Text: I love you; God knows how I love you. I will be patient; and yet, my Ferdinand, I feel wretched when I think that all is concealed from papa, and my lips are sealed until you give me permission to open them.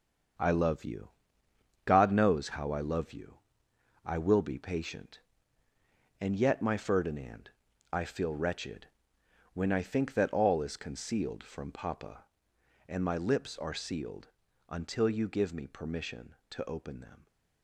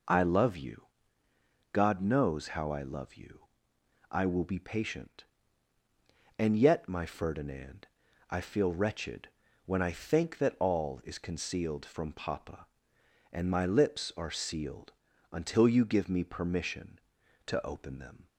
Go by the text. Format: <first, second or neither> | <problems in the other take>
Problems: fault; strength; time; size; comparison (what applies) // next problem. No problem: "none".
second | gets quieter; strong; throughout; 8.5 dB // pauses between "wretched" and "when"; noticeable; at 8.8 s; 0.66 s long; slight in the second // pauses between "sealed" and "until"; at 14.2 s; 0.40 s long; also in the second